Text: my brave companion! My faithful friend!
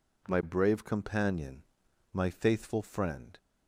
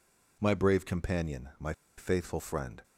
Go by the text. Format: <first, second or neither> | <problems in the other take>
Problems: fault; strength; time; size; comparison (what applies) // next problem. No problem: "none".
first | pauses between "My" and "faithful"; slight; at 1.7 s; 0.25 s long